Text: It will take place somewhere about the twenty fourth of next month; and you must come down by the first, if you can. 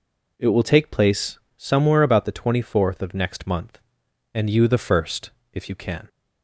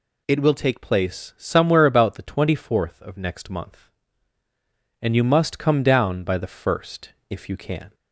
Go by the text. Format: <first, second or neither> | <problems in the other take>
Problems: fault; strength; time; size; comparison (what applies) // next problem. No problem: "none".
second | pauses between "place" and "somewhere"; slight; at 1.3 s; 0.18 s long // skips "must come down by"; at 4.6 s